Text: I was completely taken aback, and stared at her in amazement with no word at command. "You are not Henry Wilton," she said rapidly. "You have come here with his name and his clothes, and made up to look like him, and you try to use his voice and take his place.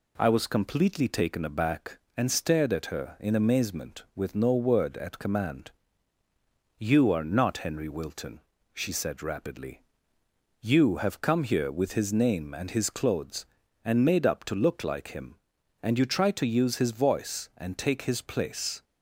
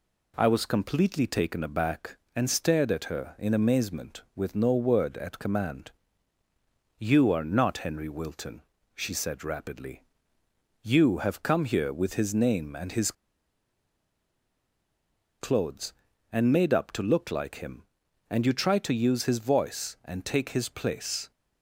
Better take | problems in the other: first | pauses between "his" and "clothes"; strong; at 13.1 s; 2.2 s long

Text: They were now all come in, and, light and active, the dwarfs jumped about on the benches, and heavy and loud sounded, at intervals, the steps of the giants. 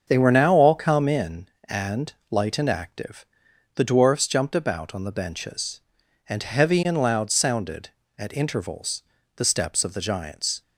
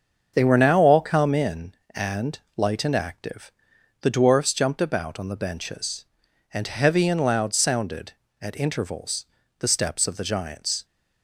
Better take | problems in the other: neither | starts louder than the rest; the same in both

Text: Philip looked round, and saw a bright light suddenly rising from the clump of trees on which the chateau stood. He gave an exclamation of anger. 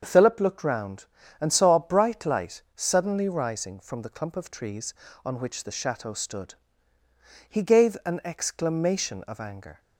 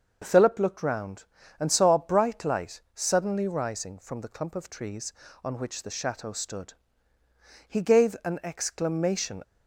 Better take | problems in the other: first | starts louder than the rest; noticeable; until 1.2 s; 6 dB; also in the first // stops before "of anger"; at 9.4 s

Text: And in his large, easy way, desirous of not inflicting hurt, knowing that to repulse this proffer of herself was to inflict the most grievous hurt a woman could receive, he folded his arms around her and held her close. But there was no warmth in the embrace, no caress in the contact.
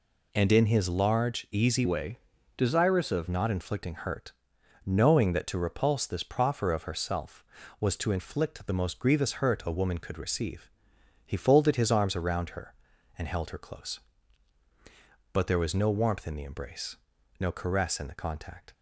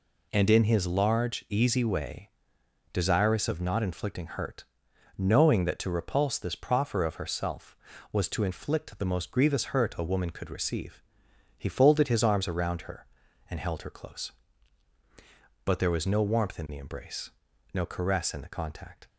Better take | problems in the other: second | changes voice from "way" to "of"; from 1.8 to 3.2 s; 1.4 s long

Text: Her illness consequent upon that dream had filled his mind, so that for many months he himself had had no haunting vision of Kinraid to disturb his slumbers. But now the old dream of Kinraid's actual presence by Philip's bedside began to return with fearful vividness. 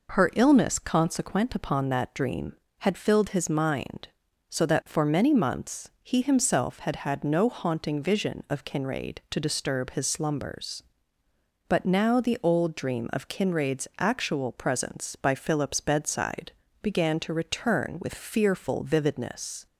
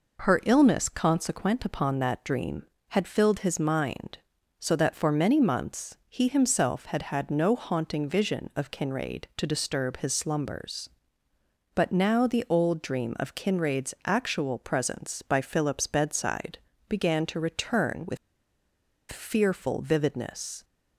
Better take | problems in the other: first | pauses between "bedside" and "began"; slight; at 16.5 s; 0.32 s long; slight in the first // pauses between "with" and "fearful"; noticeable; at 18.1 s; 0.94 s long

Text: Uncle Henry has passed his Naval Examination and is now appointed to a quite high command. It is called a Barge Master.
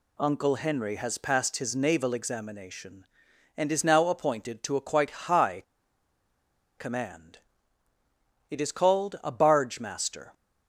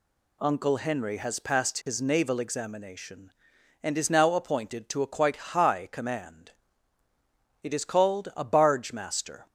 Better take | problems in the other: second | pauses between "high" and "command"; at 5.6 s; 1.1 s long

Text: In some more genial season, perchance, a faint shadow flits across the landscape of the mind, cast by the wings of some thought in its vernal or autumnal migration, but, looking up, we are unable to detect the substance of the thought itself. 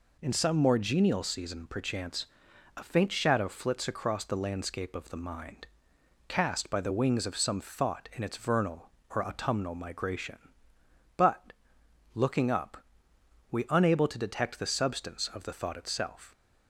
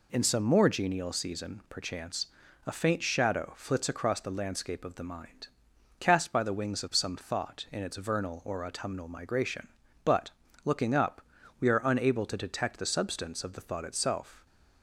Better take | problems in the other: second | skips "are"; at 13.6 s

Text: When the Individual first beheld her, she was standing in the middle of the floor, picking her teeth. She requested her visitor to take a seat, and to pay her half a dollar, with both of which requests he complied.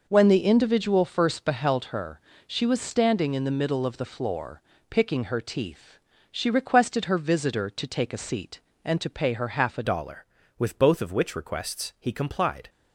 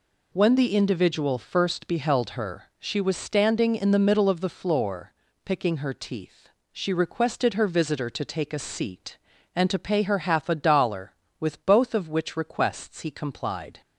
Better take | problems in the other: second | changes voice at "dollar"; from 9.8 s on; 2.8 s long

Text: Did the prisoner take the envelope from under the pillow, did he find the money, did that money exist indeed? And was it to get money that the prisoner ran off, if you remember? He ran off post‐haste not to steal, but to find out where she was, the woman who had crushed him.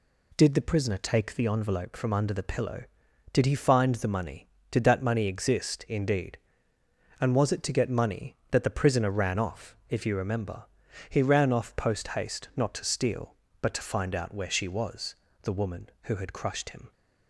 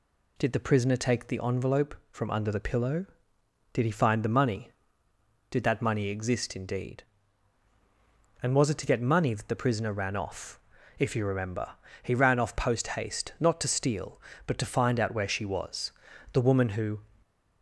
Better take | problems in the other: first | stops before "had crushed him"; at 17.2 s

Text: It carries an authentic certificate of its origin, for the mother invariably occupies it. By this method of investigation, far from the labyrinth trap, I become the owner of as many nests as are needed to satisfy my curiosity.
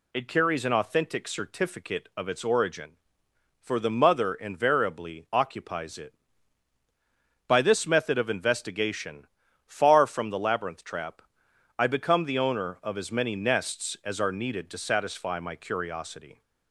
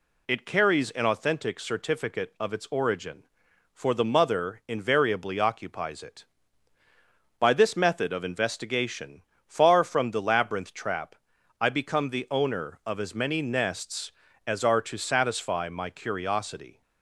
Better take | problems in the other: first | skips "needed"; at 14.8 s

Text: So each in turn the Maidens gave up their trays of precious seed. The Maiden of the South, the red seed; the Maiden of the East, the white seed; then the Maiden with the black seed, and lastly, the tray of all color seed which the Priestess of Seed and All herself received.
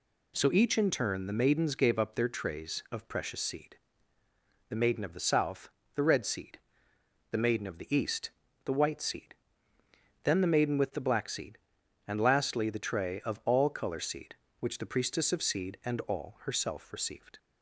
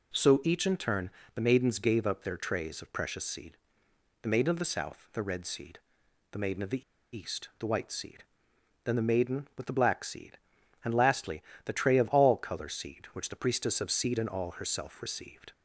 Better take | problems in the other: first | pauses between "turn" and "the"; slight; at 1.0 s; 0.26 s long // pauses between "the" and "East"; slight; at 6.8 s; 0.32 s long

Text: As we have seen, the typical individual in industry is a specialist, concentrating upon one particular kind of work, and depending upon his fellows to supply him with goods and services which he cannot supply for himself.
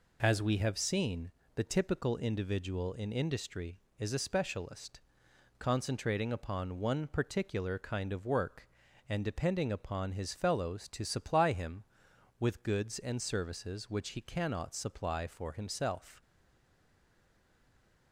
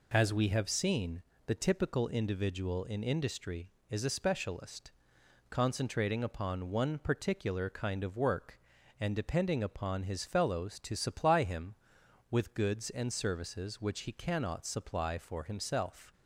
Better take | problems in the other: second | stays silent after the last word; noticeable; from 16.2 s on; 1.9 s long

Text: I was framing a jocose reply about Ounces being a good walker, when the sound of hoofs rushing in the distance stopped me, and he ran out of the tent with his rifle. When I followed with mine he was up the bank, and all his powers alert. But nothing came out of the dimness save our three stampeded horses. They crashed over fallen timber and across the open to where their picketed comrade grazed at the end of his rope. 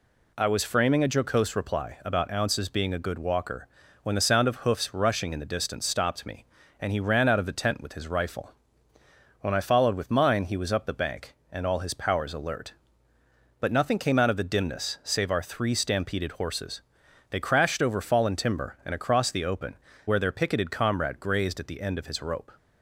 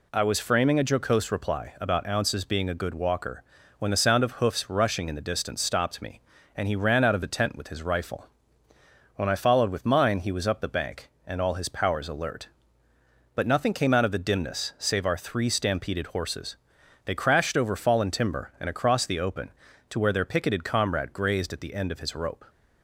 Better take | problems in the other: second | skips "to"; at 19.9 s

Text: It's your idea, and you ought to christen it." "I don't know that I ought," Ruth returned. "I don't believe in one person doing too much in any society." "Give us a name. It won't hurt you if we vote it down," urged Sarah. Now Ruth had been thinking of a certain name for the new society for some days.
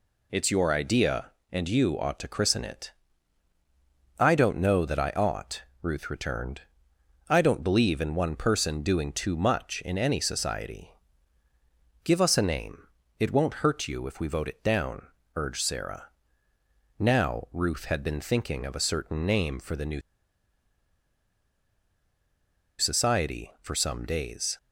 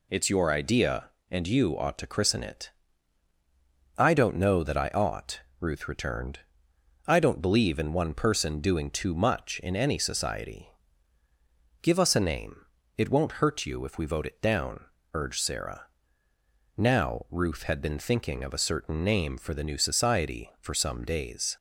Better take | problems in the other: second | pauses between "new" and "society"; strong; at 20.0 s; 2.7 s long

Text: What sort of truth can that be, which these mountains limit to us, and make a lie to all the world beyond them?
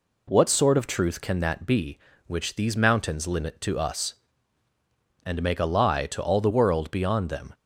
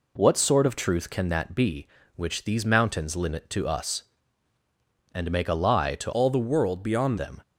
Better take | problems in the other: first | changes voice from "all" to "beyond"; from 6.1 to 7.1 s; 1.0 s long

